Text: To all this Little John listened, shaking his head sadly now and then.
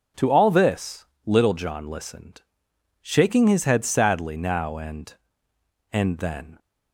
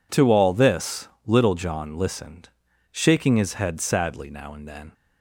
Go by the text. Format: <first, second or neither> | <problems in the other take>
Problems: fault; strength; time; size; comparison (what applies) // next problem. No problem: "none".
second | pauses between "this" and "Little"; slight; at 1.0 s; 0.18 s long; slight in the second // says "and" twice; at 5.9 s